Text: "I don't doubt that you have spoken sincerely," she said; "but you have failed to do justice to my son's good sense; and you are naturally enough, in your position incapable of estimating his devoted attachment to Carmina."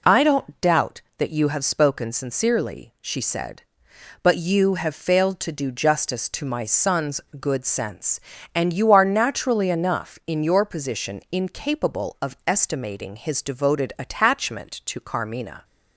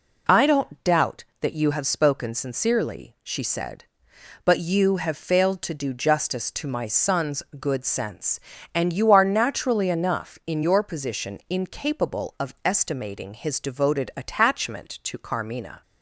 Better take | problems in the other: neither | pauses between "son's" and "good"; slight; the same in both

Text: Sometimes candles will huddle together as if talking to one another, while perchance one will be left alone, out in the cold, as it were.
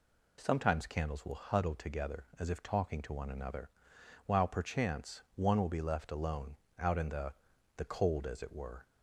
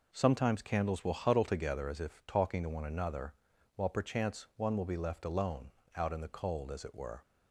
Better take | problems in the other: second | says "the" twice; at 7.7 s

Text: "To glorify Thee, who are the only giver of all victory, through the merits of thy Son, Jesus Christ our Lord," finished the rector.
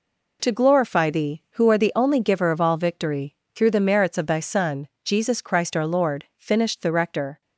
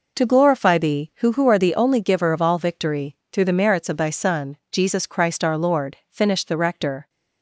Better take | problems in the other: first | says "who" twice; at 1.3 s

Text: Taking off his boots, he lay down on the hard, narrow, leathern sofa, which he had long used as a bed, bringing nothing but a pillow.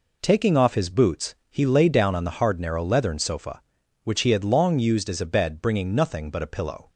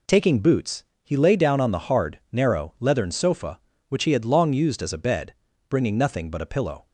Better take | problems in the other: first | skips "off his"; at 0.3 s

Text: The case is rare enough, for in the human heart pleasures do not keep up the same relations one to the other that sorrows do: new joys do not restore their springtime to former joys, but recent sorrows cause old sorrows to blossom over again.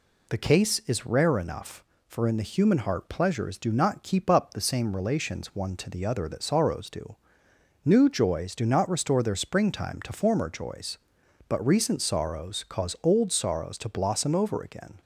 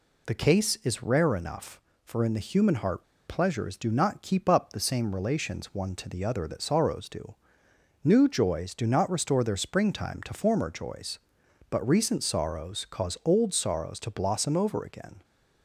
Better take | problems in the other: first | pauses between "heart" and "pleasures"; slight; at 3.0 s; 0.22 s long

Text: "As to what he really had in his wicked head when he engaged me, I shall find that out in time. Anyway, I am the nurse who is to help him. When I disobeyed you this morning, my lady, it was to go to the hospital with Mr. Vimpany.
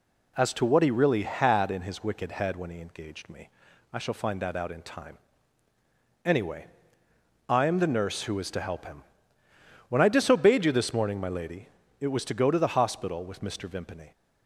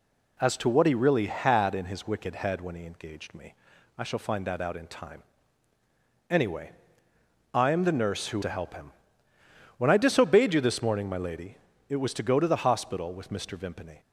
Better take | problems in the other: first | skips "is"; at 8.4 s

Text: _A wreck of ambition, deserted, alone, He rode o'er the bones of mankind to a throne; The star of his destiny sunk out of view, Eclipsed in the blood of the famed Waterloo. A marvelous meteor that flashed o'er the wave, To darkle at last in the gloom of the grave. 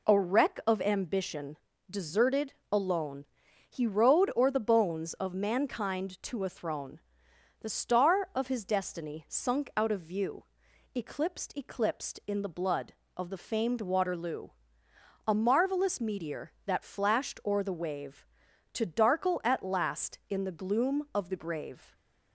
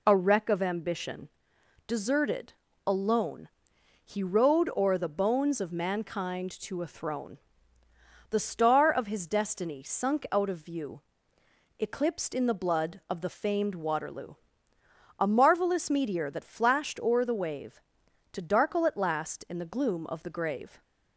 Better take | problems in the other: second | says "Eclipsed" twice; at 11.5 s

